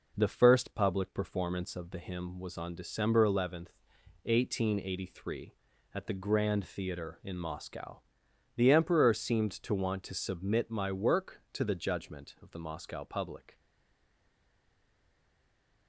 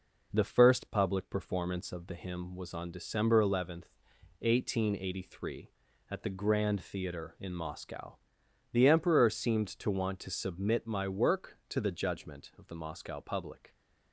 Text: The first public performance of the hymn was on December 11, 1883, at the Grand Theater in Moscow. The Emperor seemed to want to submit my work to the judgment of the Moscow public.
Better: second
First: stays silent after the last word; from 13.5 s on; 2.3 s long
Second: none

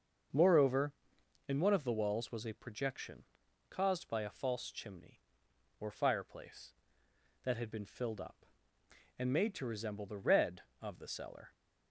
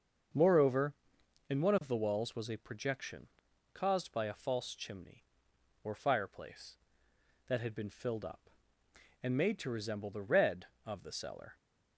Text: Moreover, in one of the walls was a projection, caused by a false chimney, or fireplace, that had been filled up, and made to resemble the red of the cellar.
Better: neither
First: starts louder than the rest; until 1.8 s; 6.5 dB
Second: starts louder than the rest; until 1.9 s; 6.5 dB

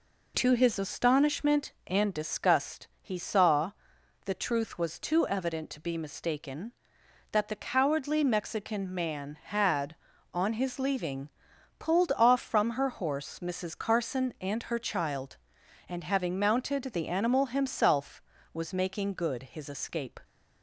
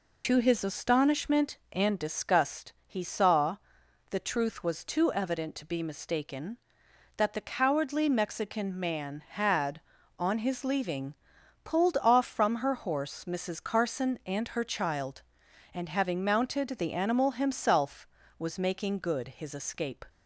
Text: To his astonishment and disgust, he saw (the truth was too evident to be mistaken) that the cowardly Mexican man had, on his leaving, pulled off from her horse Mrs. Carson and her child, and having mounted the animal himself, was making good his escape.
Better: first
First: none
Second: loses the start of "To"; at 0.2 s; 50 ms

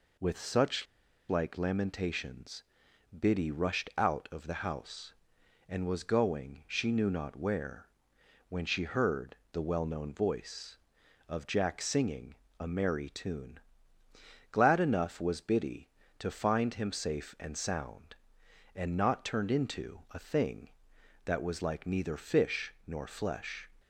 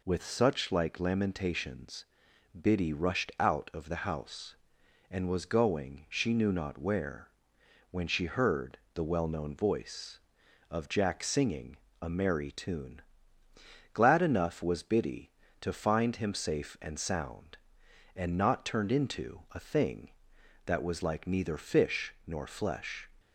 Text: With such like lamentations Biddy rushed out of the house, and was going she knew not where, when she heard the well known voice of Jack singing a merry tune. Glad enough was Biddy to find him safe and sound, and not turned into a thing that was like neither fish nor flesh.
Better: second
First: pauses between "such" and "like"; at 0.8 s; 0.43 s long // pauses between "lamentations" and "Biddy"; noticeable; at 2.6 s; 0.54 s long // pauses between "heard" and "the"; slight; at 9.3 s; 0.16 s long // pauses between "singing" and "a"; slight; at 12.3 s; 0.24 s long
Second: pauses between "lamentations" and "Biddy"; noticeable; at 2.0 s; 0.54 s long // pauses between "heard" and "the"; slight; at 8.7 s; 0.16 s long // pauses between "singing" and "a"; slight; at 11.7 s; 0.24 s long

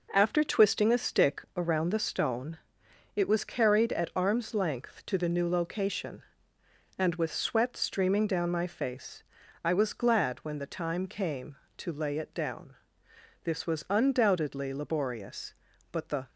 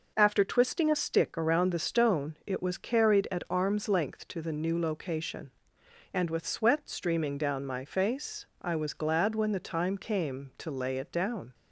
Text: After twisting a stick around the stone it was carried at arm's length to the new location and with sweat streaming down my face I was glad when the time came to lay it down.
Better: second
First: pauses between "stone" and "it"; noticeable; at 2.5 s; 0.58 s long // pauses between "face" and "I"; at 9.2 s; 0.42 s long // goes on to say "This was undoubtedly laborious but the"; strong; from 13.4 s on; 2.8 s long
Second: pauses between "face" and "I"; slight; at 8.4 s; 0.16 s long

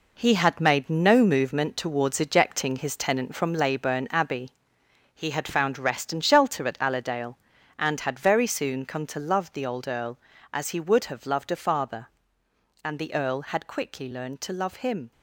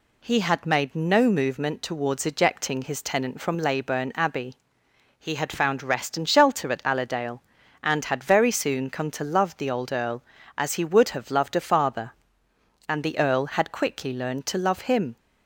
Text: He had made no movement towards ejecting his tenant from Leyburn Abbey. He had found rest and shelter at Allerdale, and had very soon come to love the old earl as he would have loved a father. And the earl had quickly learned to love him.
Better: second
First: gets quieter; strong; throughout; 8.5 dB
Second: none

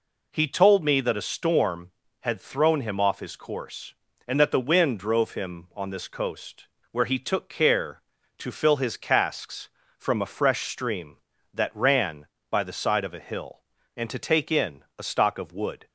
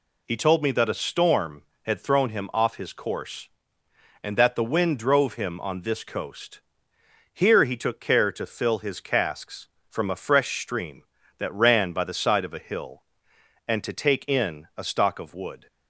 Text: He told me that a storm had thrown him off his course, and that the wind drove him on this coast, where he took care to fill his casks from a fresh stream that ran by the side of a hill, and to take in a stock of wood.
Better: first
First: none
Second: says "here" for "where"; at 7.3 s

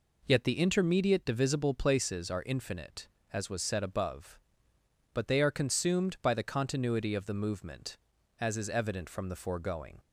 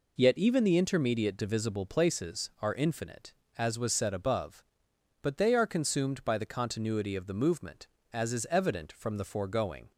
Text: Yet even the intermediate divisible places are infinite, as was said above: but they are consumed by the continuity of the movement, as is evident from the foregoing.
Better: second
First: skips "even"; at 0.4 s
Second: none

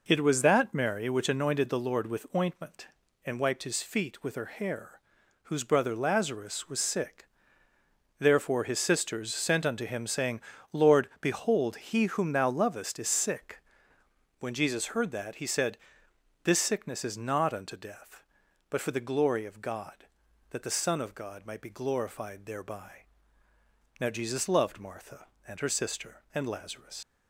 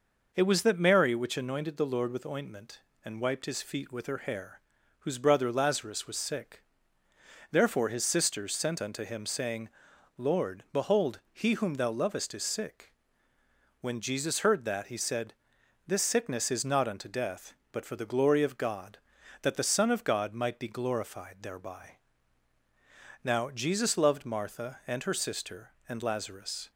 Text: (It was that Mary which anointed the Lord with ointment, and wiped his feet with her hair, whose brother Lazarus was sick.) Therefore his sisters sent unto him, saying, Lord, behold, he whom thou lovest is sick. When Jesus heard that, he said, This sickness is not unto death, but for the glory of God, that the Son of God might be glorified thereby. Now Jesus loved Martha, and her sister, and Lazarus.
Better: second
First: leaves "Lazarus" unfinished; at 27.0 s; 80 ms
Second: none

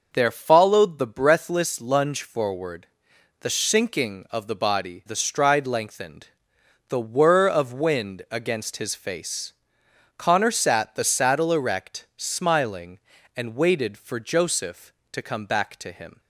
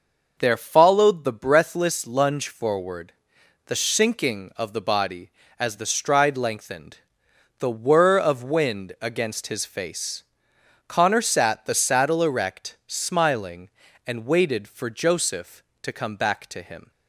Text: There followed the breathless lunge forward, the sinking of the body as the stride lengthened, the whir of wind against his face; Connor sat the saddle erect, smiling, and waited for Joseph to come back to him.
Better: second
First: skips "as"; at 5.0 s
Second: none

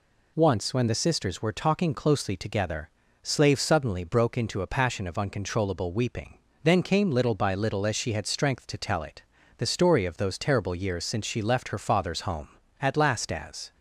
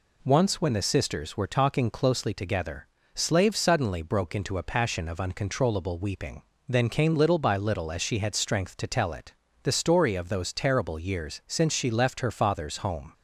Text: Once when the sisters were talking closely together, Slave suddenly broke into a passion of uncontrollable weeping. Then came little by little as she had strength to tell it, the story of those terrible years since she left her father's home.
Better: second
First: goes on to say "At last as"; noticeable; from 12.7 s on; 0.92 s long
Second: none

